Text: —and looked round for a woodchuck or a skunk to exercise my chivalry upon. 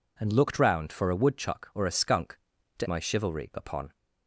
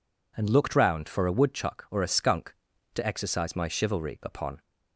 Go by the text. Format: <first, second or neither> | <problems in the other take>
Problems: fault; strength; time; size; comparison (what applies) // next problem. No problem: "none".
second | skips "exercise"; at 2.8 s